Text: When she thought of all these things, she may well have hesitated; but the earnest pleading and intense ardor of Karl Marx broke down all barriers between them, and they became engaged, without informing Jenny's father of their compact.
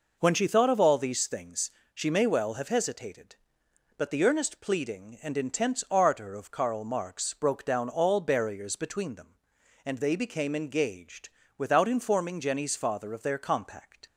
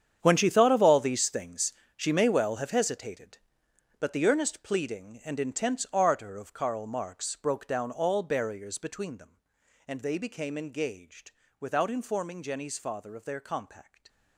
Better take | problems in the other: first | gets quieter; strong; throughout; 15 dB

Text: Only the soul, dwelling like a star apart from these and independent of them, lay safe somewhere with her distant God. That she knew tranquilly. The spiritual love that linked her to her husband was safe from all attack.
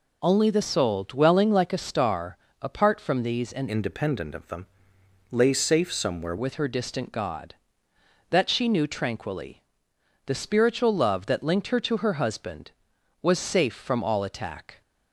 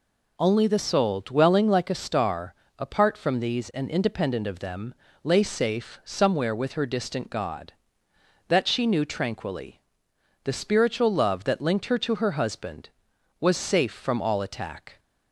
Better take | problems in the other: second | pauses between "star" and "apart"; slight; at 2.3 s; 0.22 s long; slight in the second // changes voice from "independent" to "somewhere"; from 3.6 to 6.3 s; 2.7 s long

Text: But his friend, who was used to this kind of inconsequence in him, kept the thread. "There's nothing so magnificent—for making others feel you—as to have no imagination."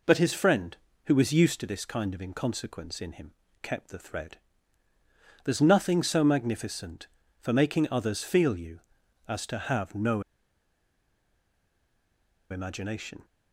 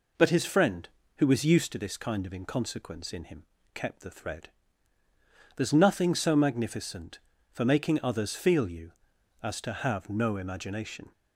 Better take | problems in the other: second | pauses between "no" and "imagination"; strong; at 10.2 s; 2.2 s long

